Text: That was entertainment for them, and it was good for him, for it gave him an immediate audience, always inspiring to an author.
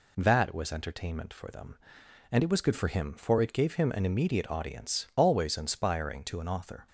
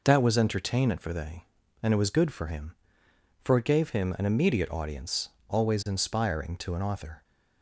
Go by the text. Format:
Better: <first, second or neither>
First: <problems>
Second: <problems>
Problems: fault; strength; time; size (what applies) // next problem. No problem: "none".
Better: first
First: none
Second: says "they" for "them"; at 1.1 s